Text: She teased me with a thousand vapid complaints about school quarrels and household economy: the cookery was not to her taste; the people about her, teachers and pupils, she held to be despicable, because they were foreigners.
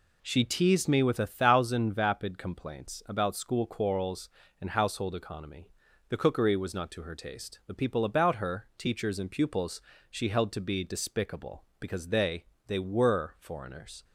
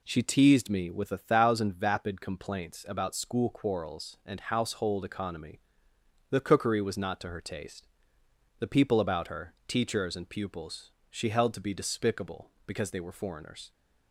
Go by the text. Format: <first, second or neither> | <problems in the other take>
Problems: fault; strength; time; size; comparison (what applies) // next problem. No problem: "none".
second | says "they" twice; at 12.6 s